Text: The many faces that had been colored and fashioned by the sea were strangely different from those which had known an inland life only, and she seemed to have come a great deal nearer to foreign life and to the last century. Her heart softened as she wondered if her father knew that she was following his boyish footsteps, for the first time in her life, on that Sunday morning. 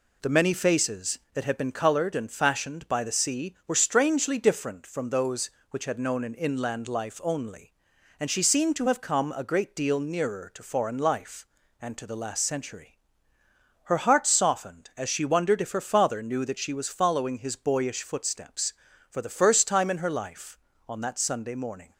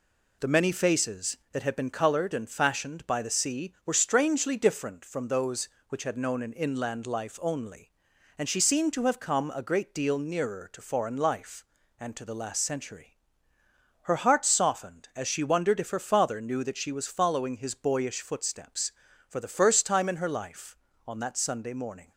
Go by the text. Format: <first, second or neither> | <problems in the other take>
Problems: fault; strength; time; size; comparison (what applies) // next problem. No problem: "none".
neither | none